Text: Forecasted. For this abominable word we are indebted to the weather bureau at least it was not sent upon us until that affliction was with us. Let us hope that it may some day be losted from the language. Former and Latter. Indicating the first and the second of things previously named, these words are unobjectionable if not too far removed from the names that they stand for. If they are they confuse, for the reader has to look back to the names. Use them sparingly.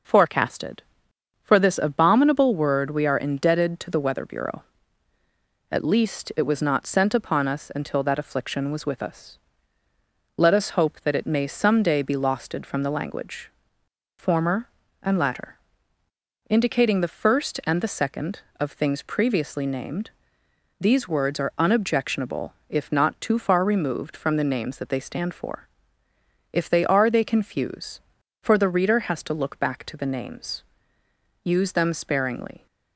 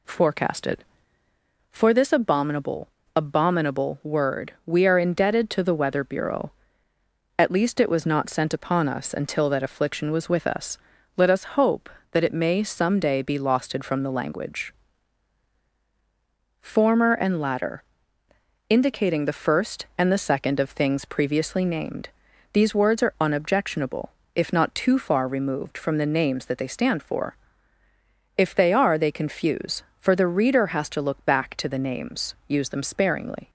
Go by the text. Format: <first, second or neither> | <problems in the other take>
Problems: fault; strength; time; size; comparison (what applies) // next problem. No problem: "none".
first | says "abominable" twice; at 3.1 s // pauses between "unobjectionable" and "if"; slight; at 24.0 s; 0.26 s long; slight in the first